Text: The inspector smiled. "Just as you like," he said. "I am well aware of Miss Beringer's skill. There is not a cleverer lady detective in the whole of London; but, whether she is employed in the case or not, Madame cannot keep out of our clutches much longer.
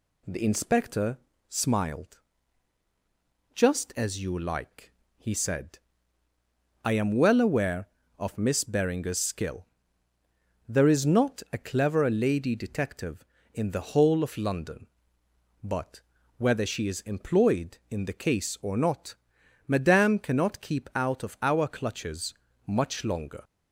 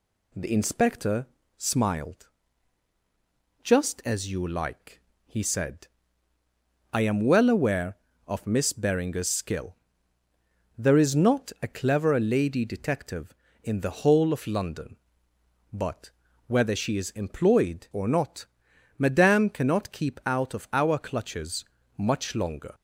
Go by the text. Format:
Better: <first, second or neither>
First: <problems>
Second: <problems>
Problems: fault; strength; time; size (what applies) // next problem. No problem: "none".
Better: first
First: pauses between "inspector" and "smiled"; slight; at 1.1 s; 0.32 s long // pauses between "clutches" and "much"; slight; at 22.3 s; 0.32 s long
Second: pauses between "inspector" and "smiled"; slight; at 1.2 s; 0.32 s long // skips "in the case"; at 17.9 s // pauses between "clutches" and "much"; slight; at 21.6 s; 0.32 s long